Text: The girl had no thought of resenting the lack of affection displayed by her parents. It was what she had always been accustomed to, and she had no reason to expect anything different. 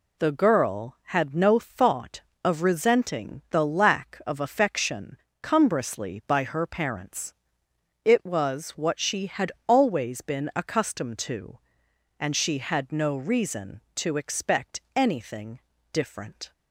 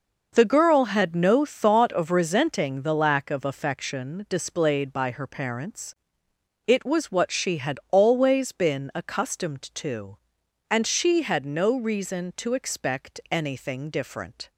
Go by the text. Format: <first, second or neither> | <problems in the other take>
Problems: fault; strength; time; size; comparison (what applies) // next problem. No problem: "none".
second | says "cumbrously" for "displayed"; at 5.4 s // pauses between "had" and "always"; slight; at 9.4 s; 0.18 s long // pauses between "expect" and "anything"; slight; at 14.7 s; 0.16 s long // pauses between "anything" and "different"; slight; at 15.5 s; 0.32 s long